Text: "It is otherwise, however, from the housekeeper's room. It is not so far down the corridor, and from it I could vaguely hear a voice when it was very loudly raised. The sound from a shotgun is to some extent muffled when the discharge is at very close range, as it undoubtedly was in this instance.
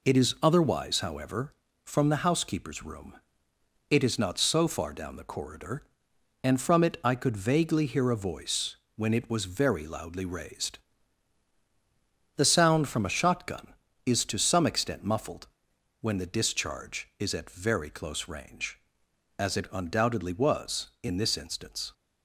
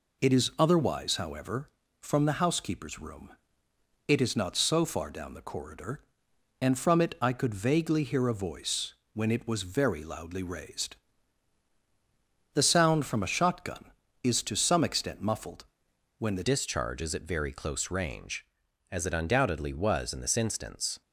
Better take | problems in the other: first | pauses between "voice" and "when"; slight; at 8.9 s; 0.18 s long; slight in the first // pauses between "muffled" and "when"; noticeable; at 15.6 s; 0.54 s long; noticeable in the first // changes voice at "discharge"; from 16.4 s on; 4.6 s long

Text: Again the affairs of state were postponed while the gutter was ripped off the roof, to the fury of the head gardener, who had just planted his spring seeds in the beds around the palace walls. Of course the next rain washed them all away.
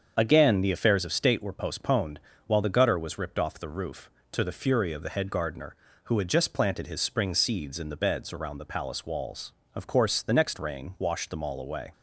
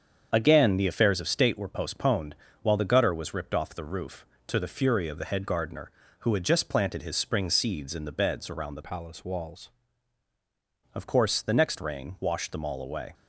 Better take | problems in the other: first | starts louder than the rest; strong; until 1.3 s; 7.5 dB; strong in the first // pauses between "postponed" and "while"; slight; at 2.3 s; 0.28 s long; slight in the first // changes voice from "palace" to "walls"; from 8.8 to 9.7 s; 0.9 s long

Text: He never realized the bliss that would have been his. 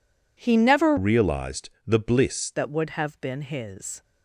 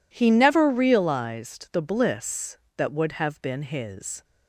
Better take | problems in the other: second | changes voice from "realized" to "bliss"; from 0.9 to 2.5 s; 1.6 s long // pauses between "realized" and "the"; slight; at 1.6 s; 0.18 s long

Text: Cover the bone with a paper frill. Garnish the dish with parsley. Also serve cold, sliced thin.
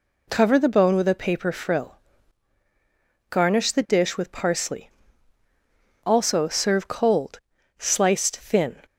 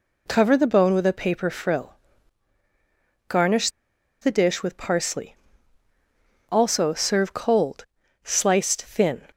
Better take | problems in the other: first | pauses between "Garnish" and "the"; noticeable; at 3.6 s; 0.52 s long

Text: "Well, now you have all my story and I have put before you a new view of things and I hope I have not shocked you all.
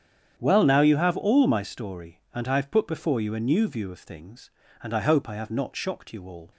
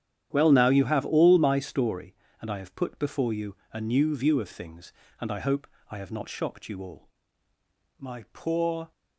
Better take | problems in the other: first | starts louder than the rest; strong; until 1.3 s; 10 dB; strong in the first // pauses between "you" and "a"; slight; at 3.5 s; 0.16 s long // pauses between "hope" and "I"; slight; at 5.6 s; 0.22 s long // goes on to say "My poor"; noticeable; from 7.9 s on; 0.92 s long

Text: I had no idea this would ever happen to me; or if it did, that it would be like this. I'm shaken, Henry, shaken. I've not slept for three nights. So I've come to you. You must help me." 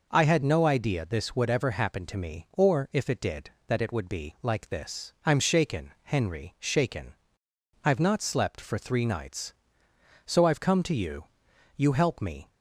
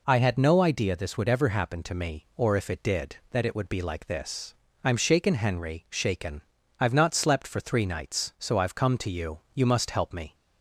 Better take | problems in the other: second | skips "must"; at 11.9 s

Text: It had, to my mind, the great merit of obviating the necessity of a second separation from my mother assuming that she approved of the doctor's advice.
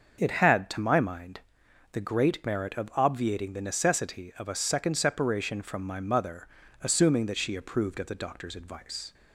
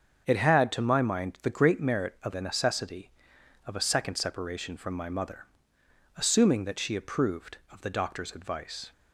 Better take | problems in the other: first | starts louder than the rest; strong; until 1.2 s; 7 dB; also in the first // skips "obviating"; at 2.3 s // pauses between "mother" and "assuming"; noticeable; at 5.4 s; 0.72 s long; slight in the first

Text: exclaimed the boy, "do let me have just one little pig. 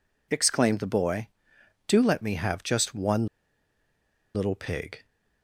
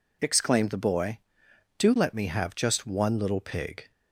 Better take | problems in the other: second | pauses between "one" and "little"; at 3.2 s; 1.0 s long

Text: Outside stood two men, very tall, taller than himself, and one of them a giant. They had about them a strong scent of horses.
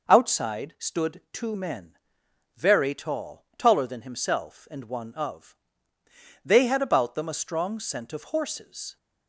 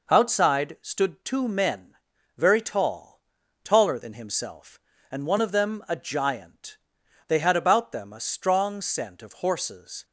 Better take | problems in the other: second | skips "them a giant"; at 5.9 s

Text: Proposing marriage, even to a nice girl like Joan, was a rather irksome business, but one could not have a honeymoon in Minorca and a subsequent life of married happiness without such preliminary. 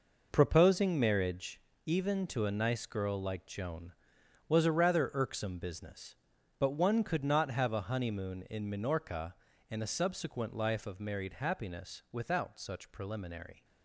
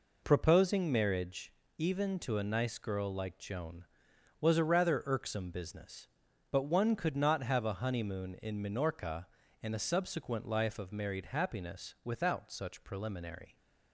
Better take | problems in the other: second | gets quieter; strong; throughout; 9.5 dB

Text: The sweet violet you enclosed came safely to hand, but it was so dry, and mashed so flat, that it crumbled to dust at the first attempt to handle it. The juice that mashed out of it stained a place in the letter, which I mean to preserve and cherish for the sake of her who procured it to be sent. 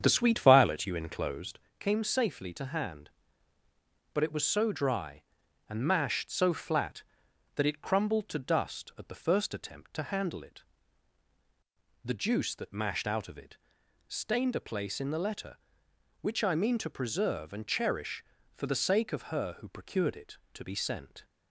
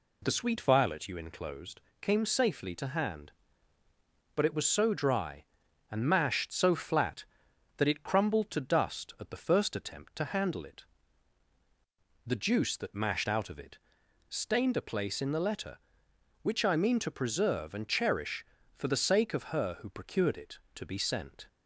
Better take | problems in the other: second | starts louder than the rest; strong; until 1.7 s; 8 dB // pauses between "enclosed" and "came"; slight; at 1.5 s; 0.18 s long; slight in the second // pauses between "it" and "stained"; noticeable; at 13.5 s; 0.50 s long; noticeable in the second

